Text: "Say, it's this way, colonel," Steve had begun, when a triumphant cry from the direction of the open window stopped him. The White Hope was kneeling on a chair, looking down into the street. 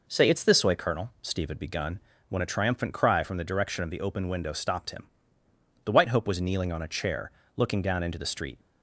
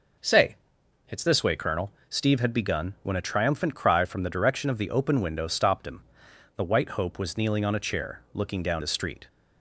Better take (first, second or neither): first